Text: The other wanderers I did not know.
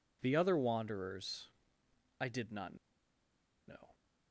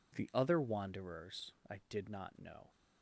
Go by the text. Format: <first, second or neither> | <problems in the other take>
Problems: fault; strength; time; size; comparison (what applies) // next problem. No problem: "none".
second | pauses between "wanderers" and "I"; noticeable; at 1.4 s; 0.72 s long // pauses between "not" and "know"; noticeable; at 2.7 s; 0.92 s long